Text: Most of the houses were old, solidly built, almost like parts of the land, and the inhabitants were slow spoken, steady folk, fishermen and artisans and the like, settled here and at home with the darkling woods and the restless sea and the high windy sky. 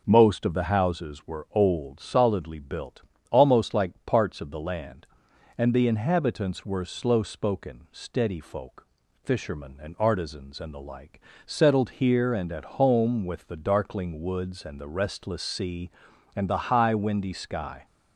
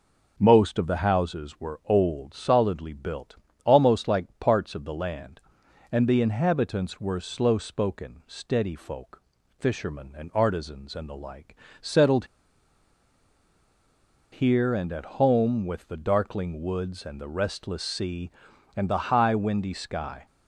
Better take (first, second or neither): first